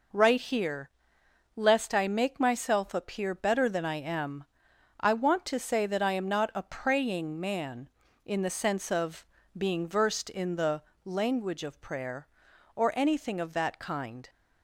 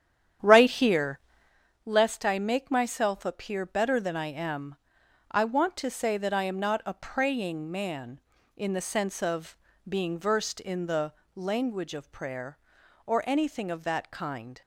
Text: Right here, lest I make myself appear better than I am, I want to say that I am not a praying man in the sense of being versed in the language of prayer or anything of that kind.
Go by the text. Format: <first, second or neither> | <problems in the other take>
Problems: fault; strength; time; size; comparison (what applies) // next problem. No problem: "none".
first | starts louder than the rest; strong; until 1.6 s; 9.5 dB // pauses between "of" and "being"; slight; at 9.5 s; 0.30 s long; slight in the first // pauses between "the" and "language"; slight; at 11.1 s; 0.22 s long; slight in the first